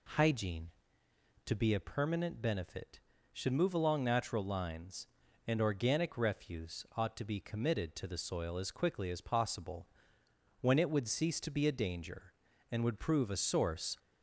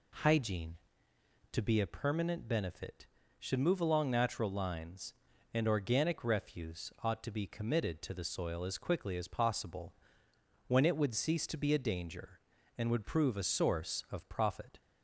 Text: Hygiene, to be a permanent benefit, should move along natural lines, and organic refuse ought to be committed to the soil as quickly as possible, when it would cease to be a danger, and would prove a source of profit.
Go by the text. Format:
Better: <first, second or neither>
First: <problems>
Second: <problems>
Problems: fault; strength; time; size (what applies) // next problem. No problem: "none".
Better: second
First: stops before "of profit"; at 13.9 s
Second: none